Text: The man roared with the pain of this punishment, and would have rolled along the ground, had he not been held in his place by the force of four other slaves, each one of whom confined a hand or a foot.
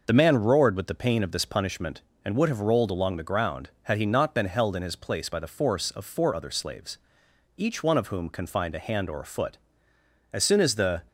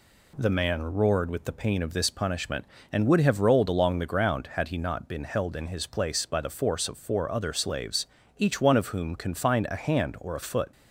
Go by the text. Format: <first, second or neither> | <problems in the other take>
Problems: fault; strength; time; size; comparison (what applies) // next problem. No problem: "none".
second | goes on to say "As soon as the"; noticeable; from 10.3 s on; 0.70 s long